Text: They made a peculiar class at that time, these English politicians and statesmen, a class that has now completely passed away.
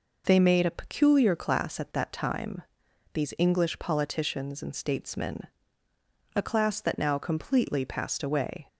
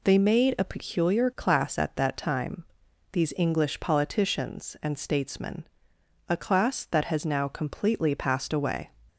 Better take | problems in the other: second | skips "has"; at 6.9 s

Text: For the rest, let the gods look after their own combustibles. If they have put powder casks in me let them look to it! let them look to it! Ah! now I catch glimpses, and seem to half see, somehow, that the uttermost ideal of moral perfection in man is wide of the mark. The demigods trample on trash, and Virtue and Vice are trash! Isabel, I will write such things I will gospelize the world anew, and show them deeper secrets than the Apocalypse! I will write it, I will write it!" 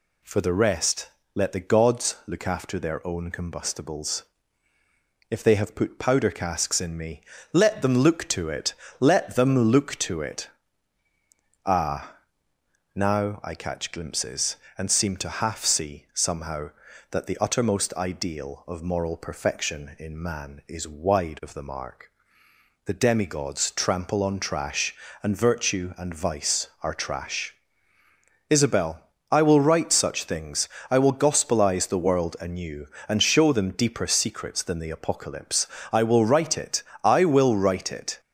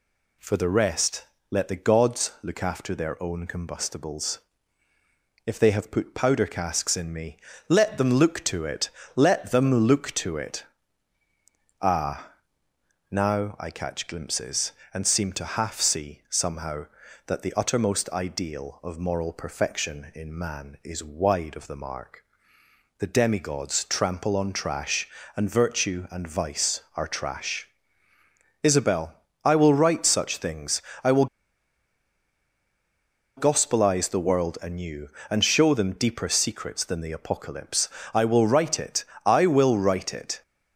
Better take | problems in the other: first | pauses between "me" and "let"; slight; at 7.3 s; 0.30 s long; slight in the first // pauses between "things" and "I"; slight; at 30.8 s; 0.20 s long; slight in the first // pauses between "will" and "gospelize"; strong; at 31.2 s; 2.1 s long

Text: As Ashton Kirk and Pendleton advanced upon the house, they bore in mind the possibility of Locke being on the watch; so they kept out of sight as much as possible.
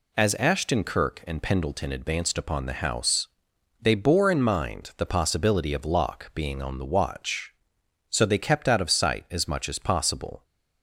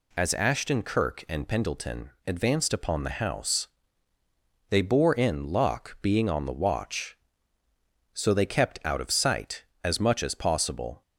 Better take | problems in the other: first | pauses between "Pendleton" and "advanced"; slight; at 2.0 s; 0.18 s long // skips "mind the possibility of"; at 5.4 s

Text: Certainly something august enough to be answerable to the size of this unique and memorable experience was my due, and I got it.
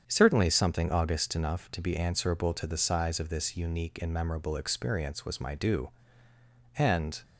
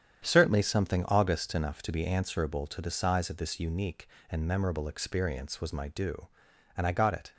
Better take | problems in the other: second | starts louder than the rest; strong; until 1.0 s; 8 dB; strong in the second // stops before "I got it"; at 7.2 s

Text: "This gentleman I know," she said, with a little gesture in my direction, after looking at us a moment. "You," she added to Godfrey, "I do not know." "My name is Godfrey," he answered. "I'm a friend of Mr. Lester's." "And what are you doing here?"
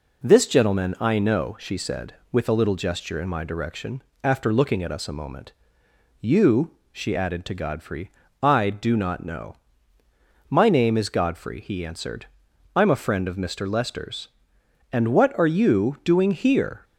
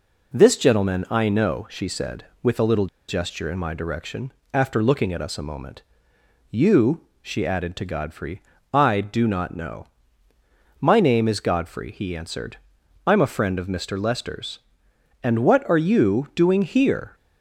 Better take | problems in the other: first | pauses between "little" and "gesture"; slight; at 2.8 s; 0.22 s long

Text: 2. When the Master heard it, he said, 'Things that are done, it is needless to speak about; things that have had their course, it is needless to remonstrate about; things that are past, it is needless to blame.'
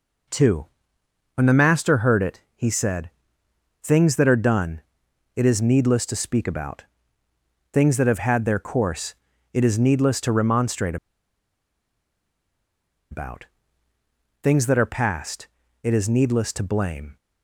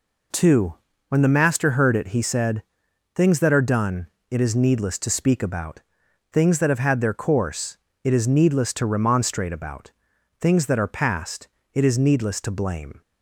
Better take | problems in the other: second | pauses between "remonstrate" and "about"; strong; at 10.9 s; 2.1 s long

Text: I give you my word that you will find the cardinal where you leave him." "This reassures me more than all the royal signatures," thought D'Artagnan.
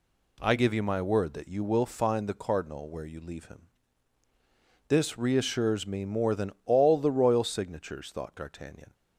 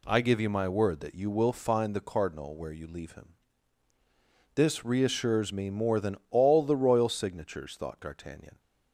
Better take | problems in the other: neither | none

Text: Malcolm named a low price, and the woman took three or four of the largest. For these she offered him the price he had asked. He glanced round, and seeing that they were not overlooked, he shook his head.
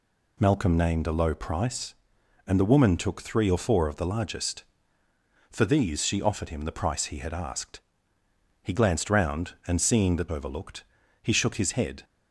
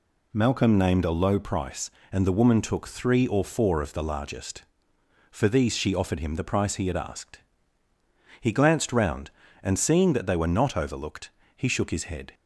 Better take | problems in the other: second | skips "they were not"; at 10.2 s

